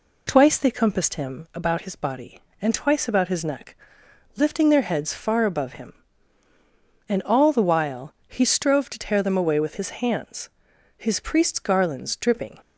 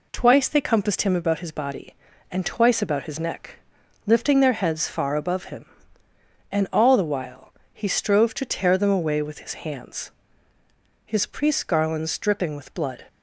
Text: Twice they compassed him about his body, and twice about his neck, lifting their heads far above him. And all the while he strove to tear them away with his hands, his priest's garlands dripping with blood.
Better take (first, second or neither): second